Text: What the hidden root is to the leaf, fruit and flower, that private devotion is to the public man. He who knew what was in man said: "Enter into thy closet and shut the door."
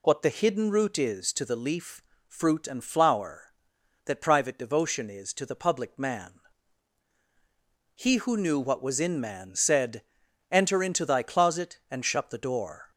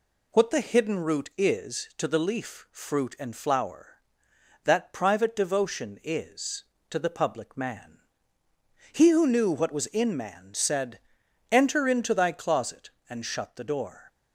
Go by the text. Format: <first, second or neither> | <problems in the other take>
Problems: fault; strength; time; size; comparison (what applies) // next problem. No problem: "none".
neither | none